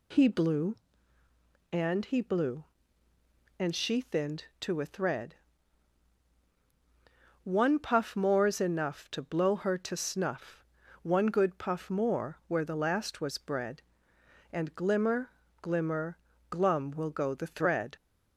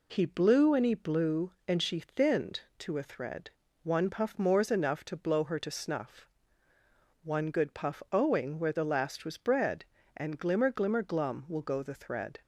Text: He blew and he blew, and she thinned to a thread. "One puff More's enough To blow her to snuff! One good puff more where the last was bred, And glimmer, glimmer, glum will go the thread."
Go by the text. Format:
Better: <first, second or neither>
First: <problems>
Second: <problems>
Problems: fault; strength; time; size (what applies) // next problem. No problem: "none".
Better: first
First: none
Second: says "owing" for "more"; at 8.1 s